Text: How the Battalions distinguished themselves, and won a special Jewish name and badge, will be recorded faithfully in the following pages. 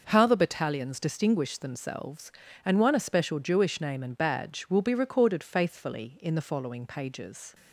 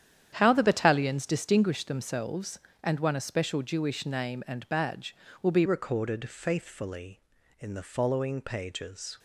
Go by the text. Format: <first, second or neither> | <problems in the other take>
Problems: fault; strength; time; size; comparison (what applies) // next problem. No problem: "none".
first | starts louder than the rest; strong; until 1.3 s; 9.5 dB // changes voice at "recorded"; from 5.6 s on; 3.5 s long